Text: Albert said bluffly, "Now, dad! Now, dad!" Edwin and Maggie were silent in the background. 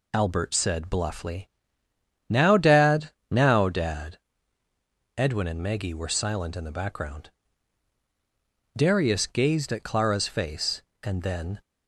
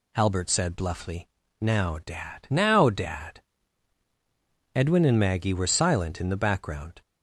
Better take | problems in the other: second | goes on to say "Darius gazed at Clara's face and then"; strong; from 8.7 s on; 2.8 s long

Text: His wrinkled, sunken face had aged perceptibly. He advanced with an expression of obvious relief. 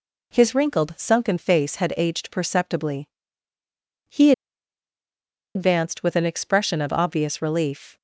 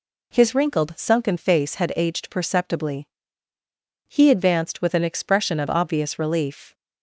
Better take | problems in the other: second | pauses between "He" and "advanced"; at 4.3 s; 1.2 s long

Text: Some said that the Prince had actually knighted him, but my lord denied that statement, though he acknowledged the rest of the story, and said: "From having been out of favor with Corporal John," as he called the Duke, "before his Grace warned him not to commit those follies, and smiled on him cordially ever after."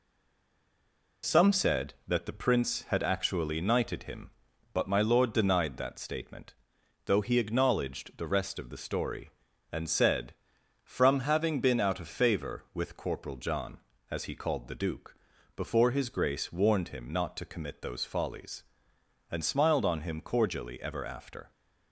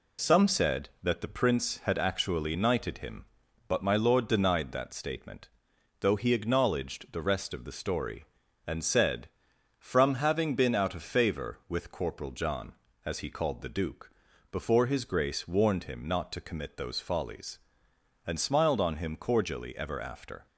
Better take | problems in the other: second | stays silent before the first word; noticeable; until 1.2 s; 1.2 s long

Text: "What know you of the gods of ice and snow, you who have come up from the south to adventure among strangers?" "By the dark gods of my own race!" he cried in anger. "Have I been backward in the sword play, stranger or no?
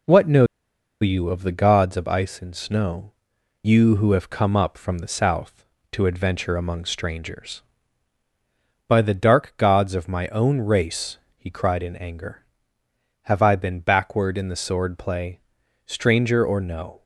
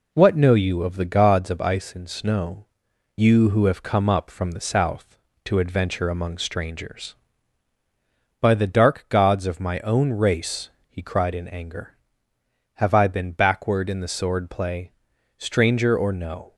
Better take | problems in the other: second | pauses between "know" and "you"; noticeable; at 0.4 s; 0.57 s long

